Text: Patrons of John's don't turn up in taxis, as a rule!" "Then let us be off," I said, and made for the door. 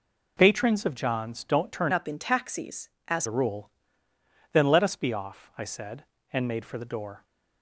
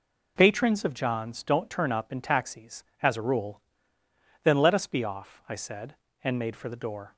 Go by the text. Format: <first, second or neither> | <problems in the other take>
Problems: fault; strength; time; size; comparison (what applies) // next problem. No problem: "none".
second | changes voice from "up" to "as"; from 1.9 to 3.2 s; 1.3 s long